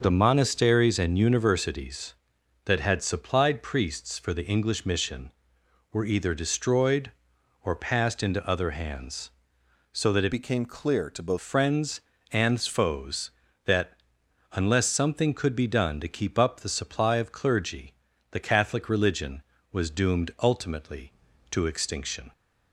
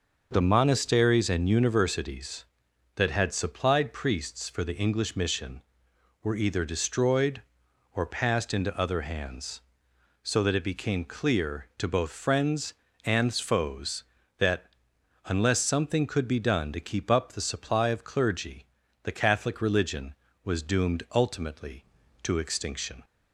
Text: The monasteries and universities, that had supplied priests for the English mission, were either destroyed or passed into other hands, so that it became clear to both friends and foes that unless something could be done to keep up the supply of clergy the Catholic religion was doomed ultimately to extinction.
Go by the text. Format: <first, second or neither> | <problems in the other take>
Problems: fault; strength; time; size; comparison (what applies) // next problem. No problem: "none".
second | starts louder than the rest; noticeable; until 1.0 s; 6 dB; noticeable in the second // changes voice from "became" to "both"; from 10.3 to 11.3 s; 1.0 s long // pauses between "that" and "unless"; noticeable; at 13.9 s; 0.60 s long; noticeable in the second // pauses between "clergy" and "the"; slight; at 17.9 s; 0.36 s long; slight in the second